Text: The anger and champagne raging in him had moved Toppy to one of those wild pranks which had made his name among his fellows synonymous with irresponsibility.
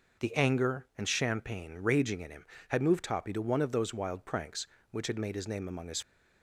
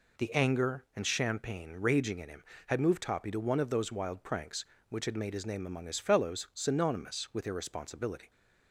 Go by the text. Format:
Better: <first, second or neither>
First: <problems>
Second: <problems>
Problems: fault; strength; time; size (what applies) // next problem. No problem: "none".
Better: second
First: stops before "fellows synonymous with irresponsibility"; at 6.0 s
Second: none